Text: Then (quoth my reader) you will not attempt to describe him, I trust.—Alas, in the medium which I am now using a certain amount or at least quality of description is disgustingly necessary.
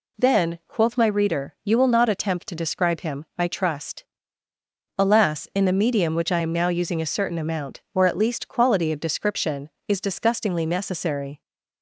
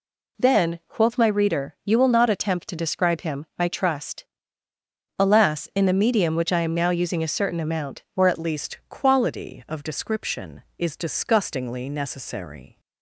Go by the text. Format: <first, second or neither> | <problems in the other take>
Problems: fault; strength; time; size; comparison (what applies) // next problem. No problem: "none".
first | changes voice at "least"; from 8.3 s on; 4.4 s long